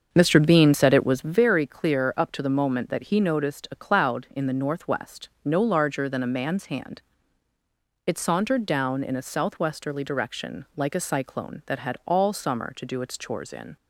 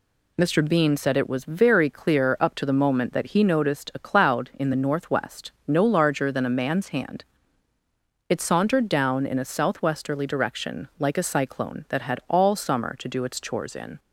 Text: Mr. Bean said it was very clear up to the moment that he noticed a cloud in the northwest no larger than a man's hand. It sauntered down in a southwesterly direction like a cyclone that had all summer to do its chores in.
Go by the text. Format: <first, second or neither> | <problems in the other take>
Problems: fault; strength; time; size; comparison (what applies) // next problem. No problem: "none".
second | starts louder than the rest; until 1.5 s; 6.5 dB // pauses between "northwest" and "no"; slight; at 5.2 s; 0.16 s long; slight in the second